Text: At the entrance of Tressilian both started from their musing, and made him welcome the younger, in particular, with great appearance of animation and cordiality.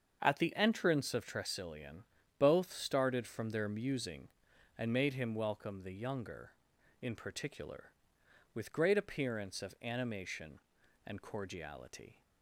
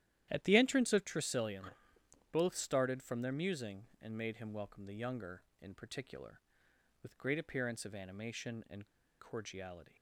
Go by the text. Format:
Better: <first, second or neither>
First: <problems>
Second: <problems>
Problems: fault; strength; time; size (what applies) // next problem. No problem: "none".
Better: first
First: starts louder than the rest; until 1.2 s; 7 dB // pauses between "Tressilian" and "both"; slight; at 2.0 s; 0.36 s long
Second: starts louder than the rest; strong; until 1.3 s; 12 dB // pauses between "Tressilian" and "both"; noticeable; at 1.7 s; 0.60 s long // pauses between "and" and "cordiality"; slight; at 8.8 s; 0.34 s long